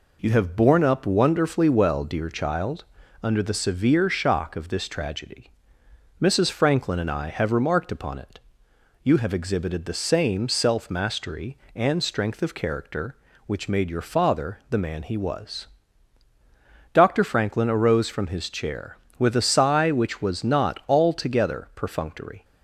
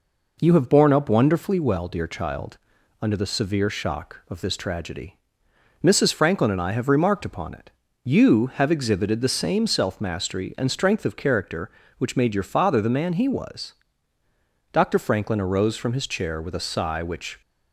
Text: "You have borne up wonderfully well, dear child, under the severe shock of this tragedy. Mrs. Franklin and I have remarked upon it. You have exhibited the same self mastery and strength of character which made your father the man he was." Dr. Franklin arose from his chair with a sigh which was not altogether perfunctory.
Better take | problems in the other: first | stops before "was not altogether perfunctory"; at 17.4 s

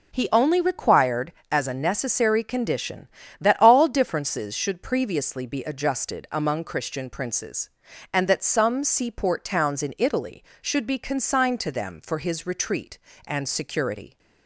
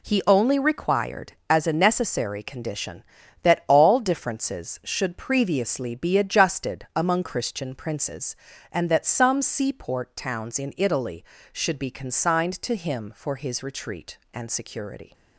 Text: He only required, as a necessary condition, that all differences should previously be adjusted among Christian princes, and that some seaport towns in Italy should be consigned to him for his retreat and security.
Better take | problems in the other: second | says "them" for "him"; at 11.7 s

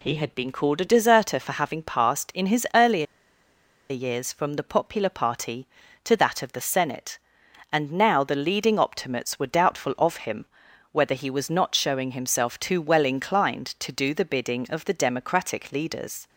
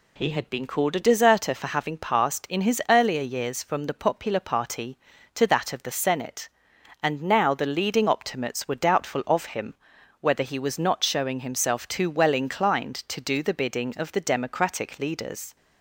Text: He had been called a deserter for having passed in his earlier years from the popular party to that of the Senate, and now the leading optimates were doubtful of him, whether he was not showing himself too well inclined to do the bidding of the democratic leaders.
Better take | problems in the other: second | pauses between "earlier" and "years"; noticeable; at 3.0 s; 0.84 s long

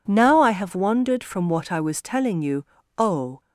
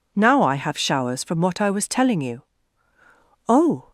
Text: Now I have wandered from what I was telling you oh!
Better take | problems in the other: first | says "showers" for "wandered"; at 0.7 s // pauses between "you" and "oh"; at 2.4 s; 1.0 s long; slight in the first

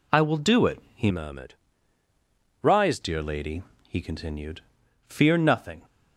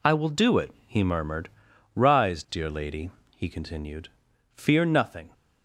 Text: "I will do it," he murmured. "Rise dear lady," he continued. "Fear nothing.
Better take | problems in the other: second | changes voice from "murmured" to "Rise"; from 1.0 to 2.9 s; 1.9 s long

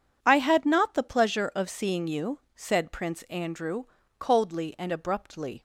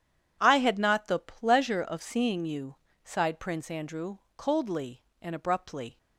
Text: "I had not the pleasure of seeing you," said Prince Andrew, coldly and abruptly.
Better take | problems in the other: first | says "sighed" for "said"; at 3.0 s

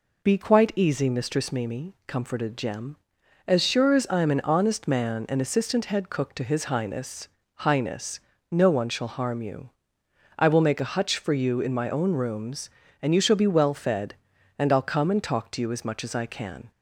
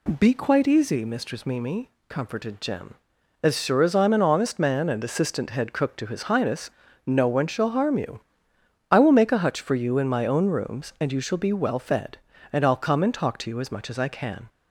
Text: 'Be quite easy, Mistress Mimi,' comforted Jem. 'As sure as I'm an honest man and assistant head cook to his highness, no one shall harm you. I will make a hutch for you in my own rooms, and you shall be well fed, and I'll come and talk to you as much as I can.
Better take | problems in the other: second | says "highness" twice; at 7.5 s

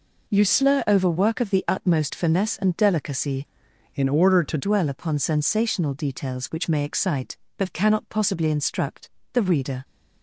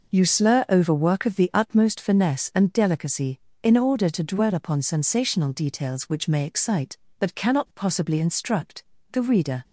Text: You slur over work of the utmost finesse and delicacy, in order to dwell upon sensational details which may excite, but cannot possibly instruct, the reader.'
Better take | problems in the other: second | changes voice from "in" to "to"; from 3.9 to 4.5 s; 0.6 s long

